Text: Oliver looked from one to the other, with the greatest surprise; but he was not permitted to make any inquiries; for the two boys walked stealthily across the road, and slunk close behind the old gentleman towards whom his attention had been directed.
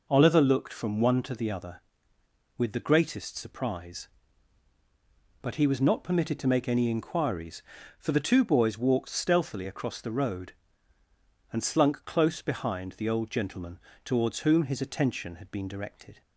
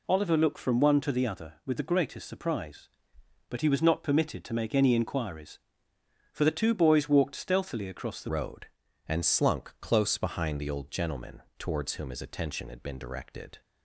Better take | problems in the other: first | changes voice at "road"; from 8.2 s on; 5.4 s long // pauses between "gentleman" and "towards"; slight; at 11.4 s; 0.16 s long; slight in the first

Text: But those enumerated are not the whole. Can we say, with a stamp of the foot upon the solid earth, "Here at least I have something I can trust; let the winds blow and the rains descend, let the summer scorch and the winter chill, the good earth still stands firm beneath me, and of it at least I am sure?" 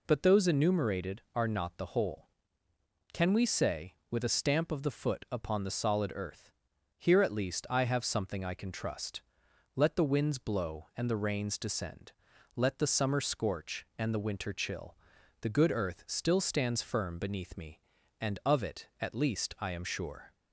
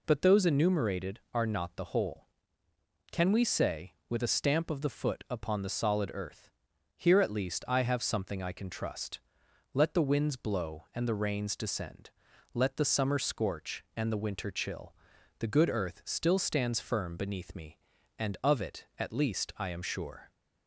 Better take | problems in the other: neither | none

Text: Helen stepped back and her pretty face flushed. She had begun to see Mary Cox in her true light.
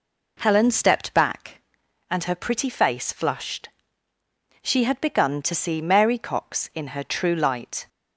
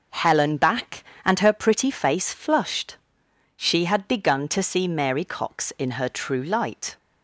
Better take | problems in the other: first | skips "stepped"; at 0.5 s

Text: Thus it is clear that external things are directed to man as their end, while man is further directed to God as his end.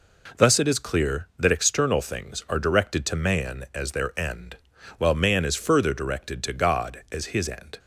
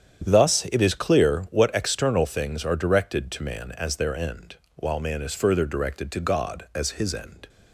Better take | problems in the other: first | starts louder than the rest; strong; until 1.3 s; 9 dB // says "what" for "that"; at 1.5 s

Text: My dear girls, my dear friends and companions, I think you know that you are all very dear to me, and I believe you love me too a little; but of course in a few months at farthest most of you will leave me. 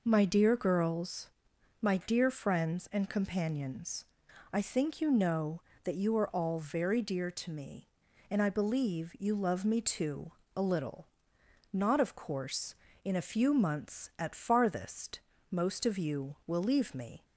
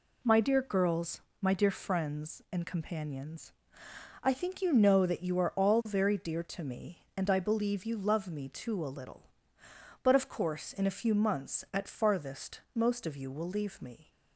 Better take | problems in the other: second | pauses between "too" and "a"; slight; at 10.3 s; 0.24 s long // says "not" for "but"; at 11.7 s // pauses between "farthest" and "most"; slight; at 15.1 s; 0.30 s long

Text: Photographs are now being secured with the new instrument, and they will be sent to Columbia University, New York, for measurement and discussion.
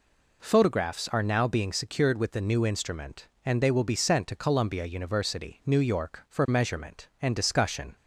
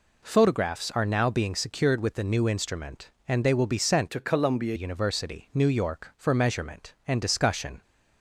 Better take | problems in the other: first | changes voice from "to" to "Columbia"; from 4.0 to 4.7 s; 0.7 s long

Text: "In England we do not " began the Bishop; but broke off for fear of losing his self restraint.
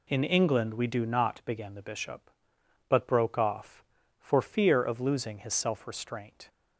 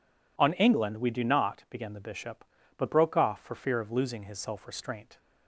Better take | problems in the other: first | says "On" for "In"; at 0.3 s

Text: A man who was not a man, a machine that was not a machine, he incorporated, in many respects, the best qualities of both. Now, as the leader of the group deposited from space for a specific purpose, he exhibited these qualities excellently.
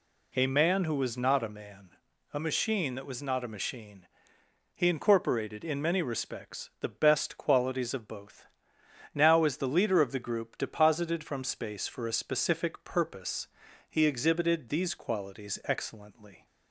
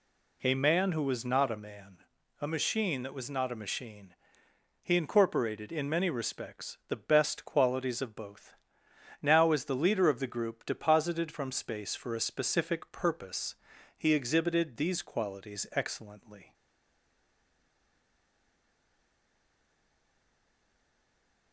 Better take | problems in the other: first | stays silent after the last word; strong; from 16.5 s on; 5.0 s long

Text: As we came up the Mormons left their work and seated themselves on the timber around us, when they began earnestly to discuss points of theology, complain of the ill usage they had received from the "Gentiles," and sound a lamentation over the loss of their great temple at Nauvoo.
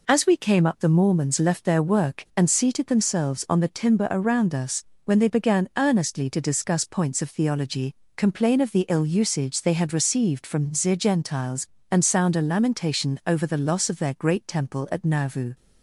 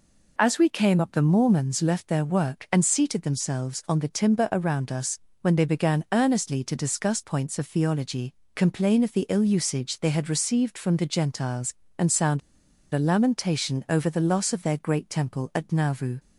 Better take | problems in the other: first | pauses between "sound" and "a"; noticeable; at 12.4 s; 0.53 s long

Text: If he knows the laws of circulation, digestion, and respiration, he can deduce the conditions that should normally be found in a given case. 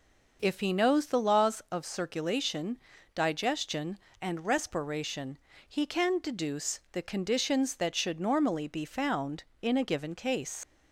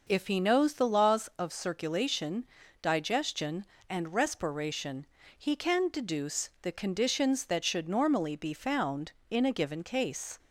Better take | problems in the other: second | leaves "case" unfinished; at 10.6 s; 65 ms

